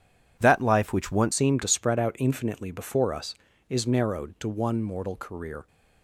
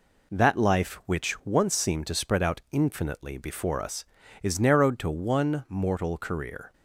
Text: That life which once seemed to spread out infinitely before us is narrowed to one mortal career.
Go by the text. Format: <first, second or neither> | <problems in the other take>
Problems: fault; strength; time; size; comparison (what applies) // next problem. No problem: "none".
second | changes voice at "seemed"; from 1.3 s on; 4.3 s long